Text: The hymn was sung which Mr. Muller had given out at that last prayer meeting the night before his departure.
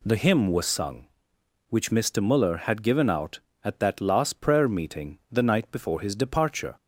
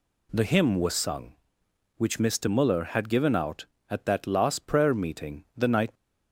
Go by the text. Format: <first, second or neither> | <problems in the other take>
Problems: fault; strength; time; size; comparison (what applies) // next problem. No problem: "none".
first | stops before "before his departure"; at 5.9 s